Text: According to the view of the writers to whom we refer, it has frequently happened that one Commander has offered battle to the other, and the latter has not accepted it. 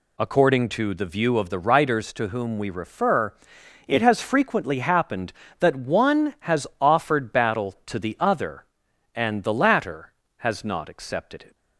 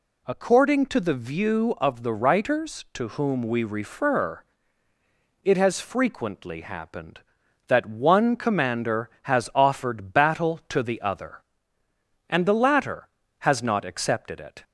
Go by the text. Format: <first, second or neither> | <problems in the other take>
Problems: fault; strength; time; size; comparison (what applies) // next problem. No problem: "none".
second | skips "Commander"; at 6.3 s